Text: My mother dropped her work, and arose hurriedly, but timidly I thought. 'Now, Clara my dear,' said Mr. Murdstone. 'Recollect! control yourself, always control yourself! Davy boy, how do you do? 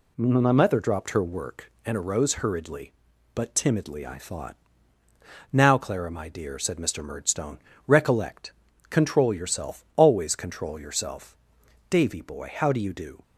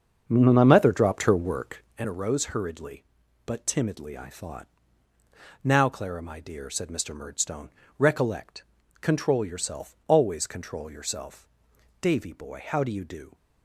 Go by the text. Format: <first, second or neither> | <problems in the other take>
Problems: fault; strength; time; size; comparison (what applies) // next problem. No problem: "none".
first | starts louder than the rest; until 2.0 s; 6.5 dB